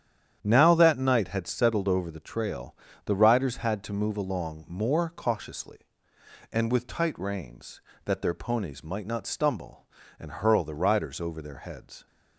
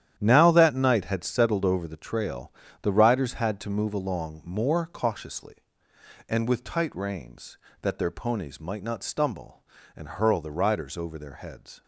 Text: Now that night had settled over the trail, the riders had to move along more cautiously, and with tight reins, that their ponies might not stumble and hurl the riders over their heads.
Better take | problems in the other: first | gets quieter; strong; throughout; 11 dB // starts louder than the rest; strong; until 1.1 s; 10.5 dB; strong in the first

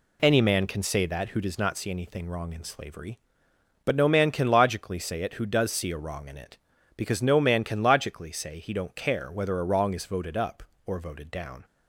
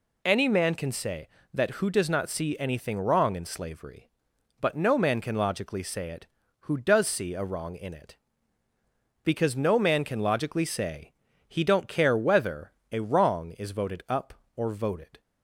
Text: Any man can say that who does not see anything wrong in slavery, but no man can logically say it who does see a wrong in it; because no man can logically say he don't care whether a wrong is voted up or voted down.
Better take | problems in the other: first | pauses between "say" and "he"; slight; at 11.1 s; 0.34 s long // pauses between "whether" and "a"; slight; at 12.7 s; 0.20 s long // stops before "down"; at 15.1 s

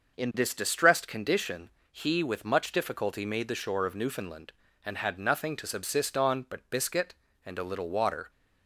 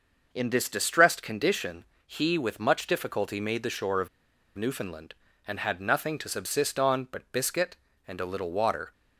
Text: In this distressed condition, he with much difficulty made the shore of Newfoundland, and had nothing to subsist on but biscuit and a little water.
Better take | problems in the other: first | starts louder than the rest; noticeable; until 1.3 s; 6 dB; noticeable in the first // pauses between "of" and "Newfoundland"; noticeable; at 4.0 s; 0.47 s long

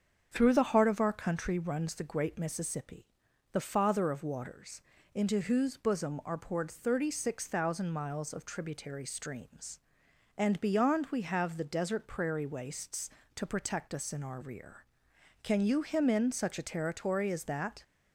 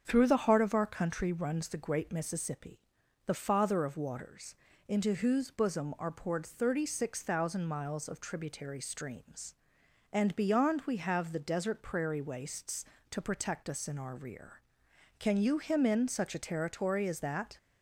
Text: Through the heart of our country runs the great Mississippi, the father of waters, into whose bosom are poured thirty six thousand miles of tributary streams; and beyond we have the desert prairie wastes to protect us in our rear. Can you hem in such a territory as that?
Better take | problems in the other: neither | starts louder than the rest; strong; the same in both

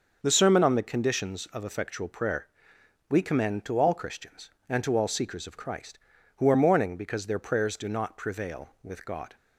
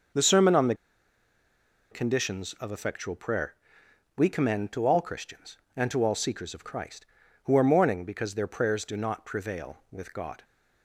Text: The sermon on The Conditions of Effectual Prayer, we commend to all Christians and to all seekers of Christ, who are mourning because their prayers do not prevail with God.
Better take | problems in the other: first | starts louder than the rest; until 2.3 s; 6.5 dB; also in the first // pauses between "The" and "Conditions"; at 0.7 s; 1.1 s long

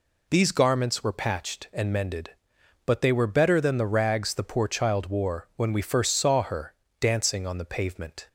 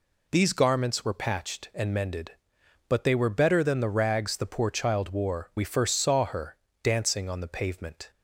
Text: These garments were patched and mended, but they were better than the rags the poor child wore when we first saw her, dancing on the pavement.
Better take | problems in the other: first | skips "when"; at 5.5 s

